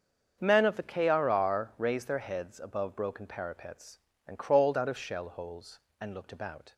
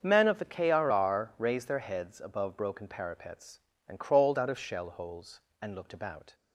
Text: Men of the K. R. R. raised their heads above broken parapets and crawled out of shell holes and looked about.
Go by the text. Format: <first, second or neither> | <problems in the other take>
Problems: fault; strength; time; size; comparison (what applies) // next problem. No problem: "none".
neither | starts louder than the rest; the same in both